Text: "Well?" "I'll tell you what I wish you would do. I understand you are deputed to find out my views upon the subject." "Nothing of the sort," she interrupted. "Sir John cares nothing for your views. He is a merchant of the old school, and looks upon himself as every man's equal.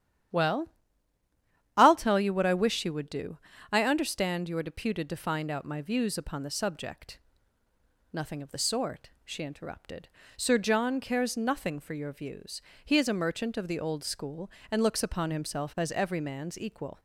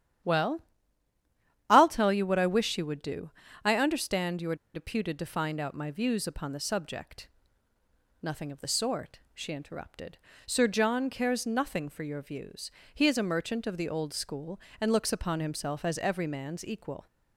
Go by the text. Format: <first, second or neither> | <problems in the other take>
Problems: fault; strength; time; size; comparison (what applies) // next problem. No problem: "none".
first | starts louder than the rest; strong; until 2.3 s; 10.5 dB; strong in the first // pauses between "are" and "deputed"; slight; at 4.5 s; 0.19 s long